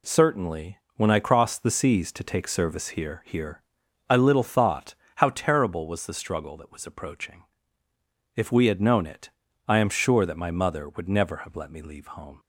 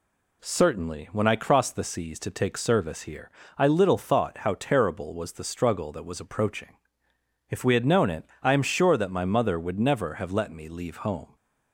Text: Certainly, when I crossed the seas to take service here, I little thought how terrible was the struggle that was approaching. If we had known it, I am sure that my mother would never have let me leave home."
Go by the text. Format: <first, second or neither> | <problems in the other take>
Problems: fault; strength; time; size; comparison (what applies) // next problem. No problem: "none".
second | says "here" twice; at 3.2 s // pauses between "thought" and "how"; slight; at 4.9 s; 0.22 s long